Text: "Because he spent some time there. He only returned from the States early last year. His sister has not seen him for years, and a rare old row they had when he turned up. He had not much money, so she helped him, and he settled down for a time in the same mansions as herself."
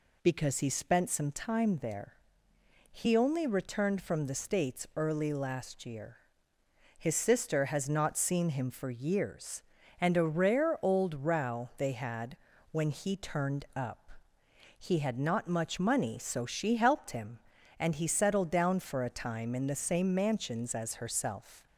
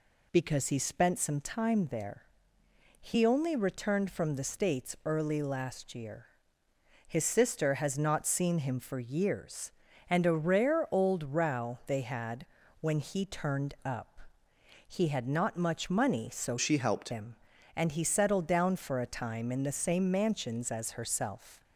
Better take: first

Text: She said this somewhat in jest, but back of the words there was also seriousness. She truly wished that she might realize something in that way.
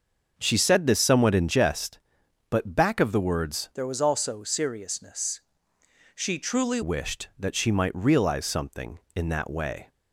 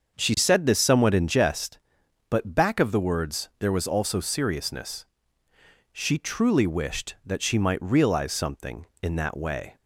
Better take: second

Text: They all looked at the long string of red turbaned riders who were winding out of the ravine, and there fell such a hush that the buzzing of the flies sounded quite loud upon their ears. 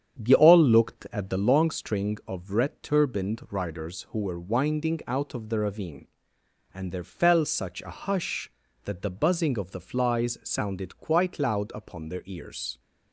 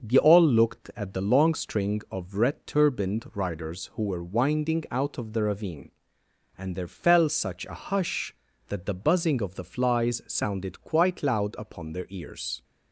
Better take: second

